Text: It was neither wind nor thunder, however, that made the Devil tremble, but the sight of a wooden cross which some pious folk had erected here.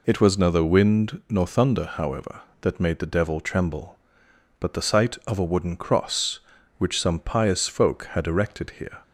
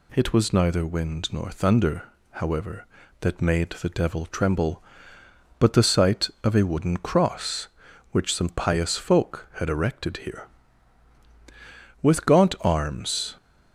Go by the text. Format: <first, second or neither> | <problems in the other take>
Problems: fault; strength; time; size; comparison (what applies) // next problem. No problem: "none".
first | goes on to say "With gaunt arms"; from 12.0 s on; 1.3 s long